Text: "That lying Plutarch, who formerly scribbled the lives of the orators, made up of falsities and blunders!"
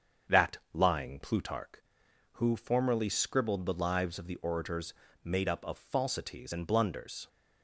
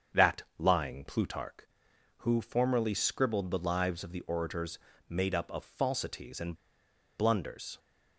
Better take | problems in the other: first | starts louder than the rest; strong; until 1.3 s; 7.5 dB; strong in the first // pauses between "That" and "lying"; slight; at 0.4 s; 0.16 s long; slight in the first // pauses between "and" and "blunders"; noticeable; at 6.5 s; 0.64 s long

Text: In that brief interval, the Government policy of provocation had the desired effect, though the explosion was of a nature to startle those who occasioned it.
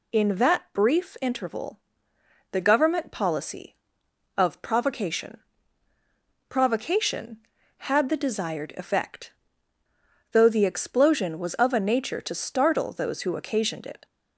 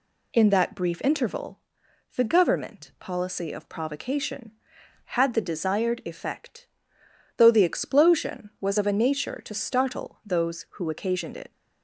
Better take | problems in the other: second | says "provocation" twice; at 6.4 s

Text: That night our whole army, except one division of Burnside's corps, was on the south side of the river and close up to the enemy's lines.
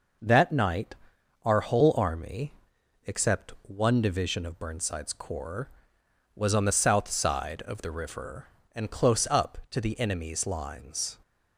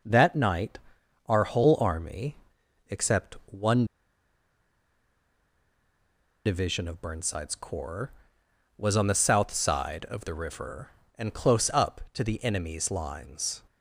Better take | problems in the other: first | pauses between "night" and "our"; noticeable; at 0.7 s; 0.50 s long; noticeable in the first // pauses between "one" and "division"; strong; at 3.8 s; 2.6 s long

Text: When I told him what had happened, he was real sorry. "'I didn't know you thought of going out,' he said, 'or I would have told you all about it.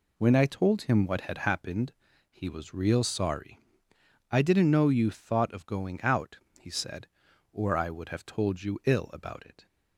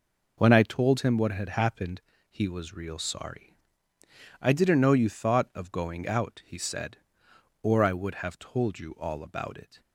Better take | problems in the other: second | says "ill" for "all"; at 8.8 s

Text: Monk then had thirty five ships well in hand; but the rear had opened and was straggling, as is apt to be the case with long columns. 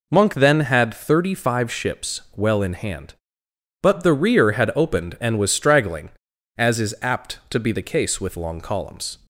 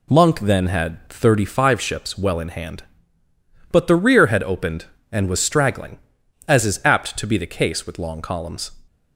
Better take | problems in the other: neither | none

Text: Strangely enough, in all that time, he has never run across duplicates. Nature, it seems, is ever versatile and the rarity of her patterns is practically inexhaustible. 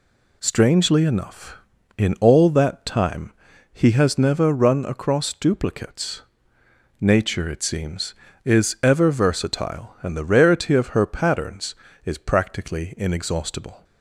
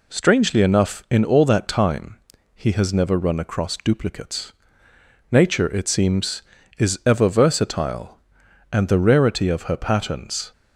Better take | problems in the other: first | stops before "is practically inexhaustible"; at 10.5 s

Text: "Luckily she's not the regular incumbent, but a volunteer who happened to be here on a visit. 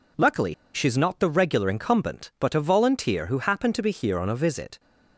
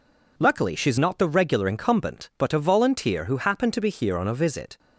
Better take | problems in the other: second | pauses between "Luckily" and "she's"; slight; at 0.5 s; 0.20 s long

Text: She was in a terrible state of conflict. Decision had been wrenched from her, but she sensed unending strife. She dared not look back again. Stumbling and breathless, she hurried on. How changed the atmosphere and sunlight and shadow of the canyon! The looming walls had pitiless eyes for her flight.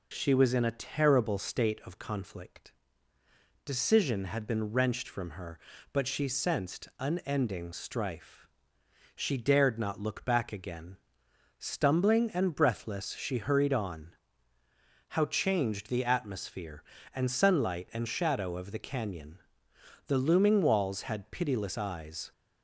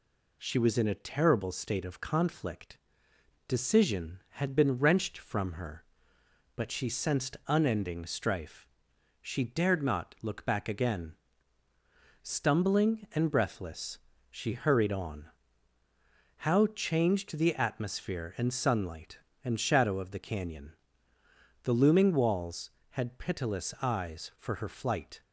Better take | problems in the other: second | stops before "for her flight"; at 22.3 s

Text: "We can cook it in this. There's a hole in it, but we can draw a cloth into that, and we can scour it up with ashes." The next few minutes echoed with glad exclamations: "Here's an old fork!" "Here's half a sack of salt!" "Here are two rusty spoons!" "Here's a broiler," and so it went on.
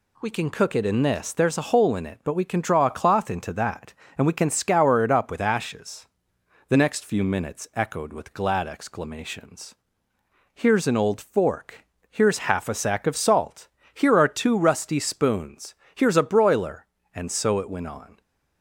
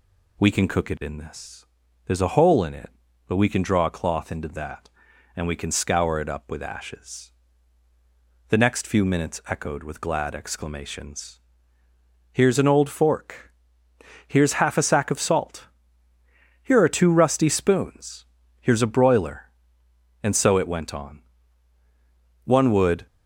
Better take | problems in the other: first | goes on to say "One would"; noticeable; from 22.4 s on; 0.62 s long

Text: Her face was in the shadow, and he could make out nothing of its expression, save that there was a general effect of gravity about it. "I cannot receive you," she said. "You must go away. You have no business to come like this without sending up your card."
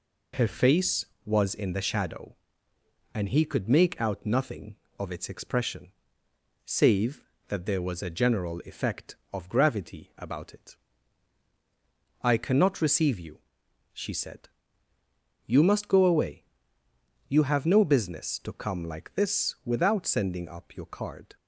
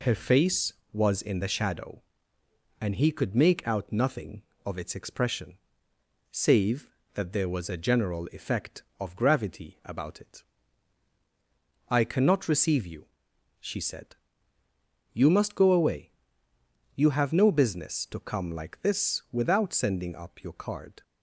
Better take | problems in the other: neither | none

